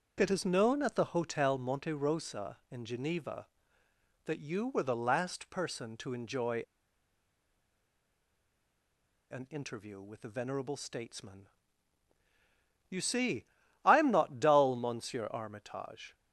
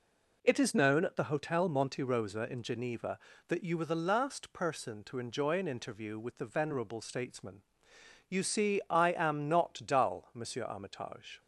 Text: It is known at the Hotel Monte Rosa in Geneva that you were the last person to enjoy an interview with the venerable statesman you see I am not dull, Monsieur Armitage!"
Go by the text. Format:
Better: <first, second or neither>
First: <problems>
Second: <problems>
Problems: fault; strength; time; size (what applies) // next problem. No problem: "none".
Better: second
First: starts louder than the rest; noticeable; until 1.1 s; 6 dB // pauses between "enjoy" and "an"; strong; at 6.6 s; 2.7 s long // pauses between "statesman" and "you"; strong; at 11.4 s; 1.4 s long // pauses between "see" and "I"; at 13.4 s; 0.42 s long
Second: pauses between "statesman" and "you"; noticeable; at 7.6 s; 0.70 s long